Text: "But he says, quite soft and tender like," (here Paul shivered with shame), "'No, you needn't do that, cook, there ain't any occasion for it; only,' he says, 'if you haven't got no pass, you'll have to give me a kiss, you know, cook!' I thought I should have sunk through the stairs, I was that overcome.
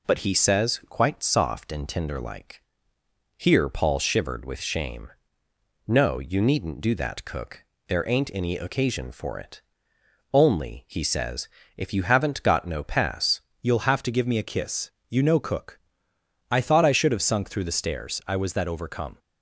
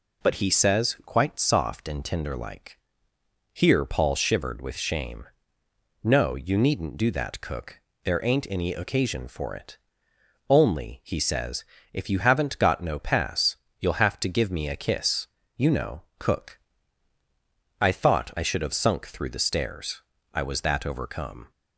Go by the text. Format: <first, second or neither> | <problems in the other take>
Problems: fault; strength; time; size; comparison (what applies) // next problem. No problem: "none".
second | changes voice at "you'll"; from 13.6 s on; 5.5 s long